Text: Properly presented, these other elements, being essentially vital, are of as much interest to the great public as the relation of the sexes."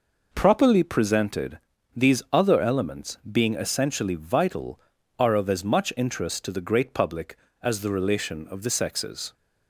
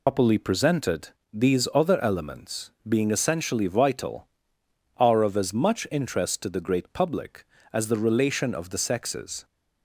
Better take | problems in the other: first | loses the start of "Properly"; at 0.0 s; 90 ms

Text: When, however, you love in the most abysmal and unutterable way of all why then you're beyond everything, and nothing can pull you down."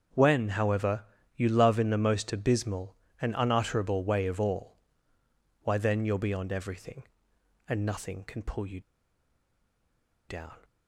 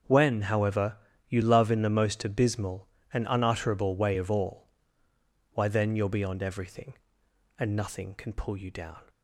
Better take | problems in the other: second | starts louder than the rest; until 1.4 s; 6.5 dB; also in the second // pauses between "all" and "why"; noticeable; at 4.7 s; 0.86 s long; noticeable in the second // pauses between "you" and "down"; strong; at 8.8 s; 1.4 s long

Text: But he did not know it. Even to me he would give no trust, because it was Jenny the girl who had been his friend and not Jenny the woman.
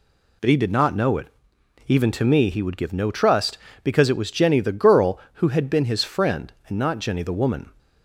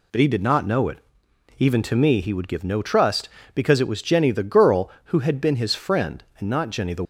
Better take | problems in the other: first | stops before "woman"; at 7.0 s

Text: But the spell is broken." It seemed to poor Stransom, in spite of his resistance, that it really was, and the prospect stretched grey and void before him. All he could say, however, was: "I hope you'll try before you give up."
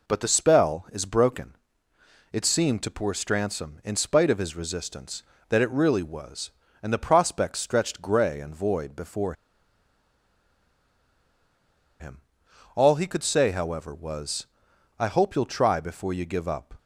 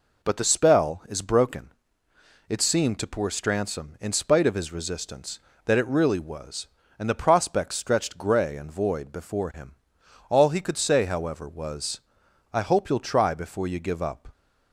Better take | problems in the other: second | pauses between "before" and "him"; strong; at 9.3 s; 2.6 s long

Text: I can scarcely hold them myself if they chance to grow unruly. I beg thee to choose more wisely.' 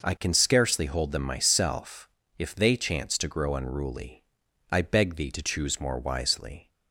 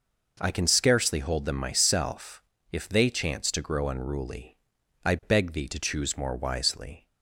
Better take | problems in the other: neither | pauses between "myself" and "if"; slight; the same in both

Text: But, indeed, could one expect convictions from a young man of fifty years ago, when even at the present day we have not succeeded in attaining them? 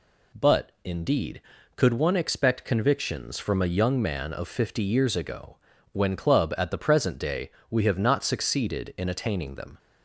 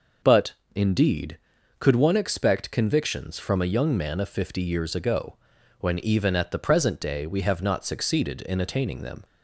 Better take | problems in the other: second | says "club" for "even"; at 6.1 s // pauses between "day" and "we"; slight; at 7.4 s; 0.20 s long

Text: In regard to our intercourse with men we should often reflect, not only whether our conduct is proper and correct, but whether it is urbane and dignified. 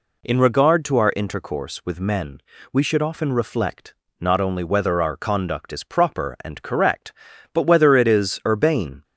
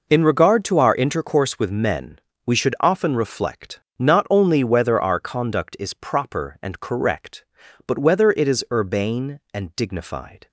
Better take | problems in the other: second | pauses between "men" and "we"; slight; at 2.4 s; 0.32 s long; slight in the second // stops before "and dignified"; at 9.0 s

